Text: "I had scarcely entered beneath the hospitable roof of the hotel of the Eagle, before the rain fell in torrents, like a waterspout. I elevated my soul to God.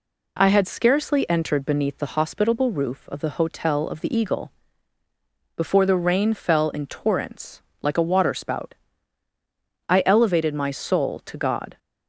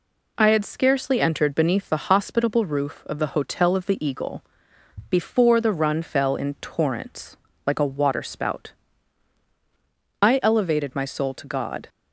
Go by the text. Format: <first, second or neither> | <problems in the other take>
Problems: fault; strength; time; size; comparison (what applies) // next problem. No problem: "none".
first | says "run" for "rain"; at 5.7 s